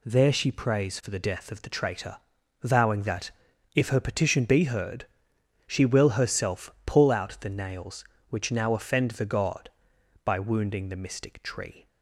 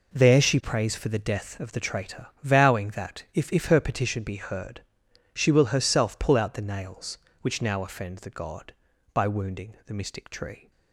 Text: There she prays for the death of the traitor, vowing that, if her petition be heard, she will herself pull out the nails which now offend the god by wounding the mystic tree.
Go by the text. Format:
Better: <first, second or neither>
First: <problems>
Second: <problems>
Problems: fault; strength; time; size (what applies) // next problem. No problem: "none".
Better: first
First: none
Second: says "if" twice; at 3.5 s